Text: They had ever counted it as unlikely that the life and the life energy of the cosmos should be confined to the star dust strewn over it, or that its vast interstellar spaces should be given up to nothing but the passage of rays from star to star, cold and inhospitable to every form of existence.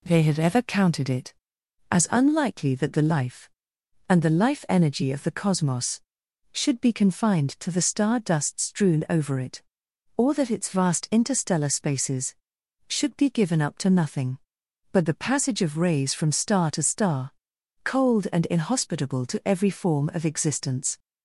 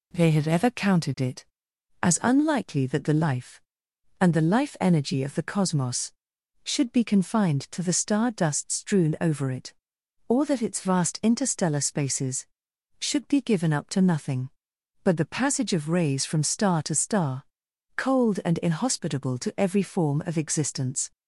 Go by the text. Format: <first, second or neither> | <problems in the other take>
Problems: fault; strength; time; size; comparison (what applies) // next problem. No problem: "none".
neither | none